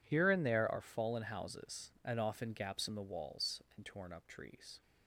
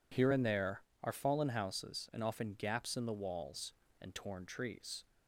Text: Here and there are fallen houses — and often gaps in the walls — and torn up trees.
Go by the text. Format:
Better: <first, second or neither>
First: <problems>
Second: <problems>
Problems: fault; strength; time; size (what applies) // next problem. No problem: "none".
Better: first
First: none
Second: skips "up"; at 4.4 s